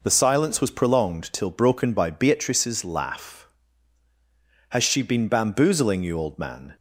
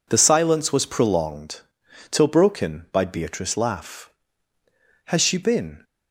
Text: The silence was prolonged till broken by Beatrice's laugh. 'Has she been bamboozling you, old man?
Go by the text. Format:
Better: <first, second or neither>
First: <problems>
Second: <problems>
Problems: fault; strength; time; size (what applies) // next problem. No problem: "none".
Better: first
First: none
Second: pauses between "prolonged" and "till"; noticeable; at 1.5 s; 0.50 s long // stops before "bamboozling you old man"; at 5.8 s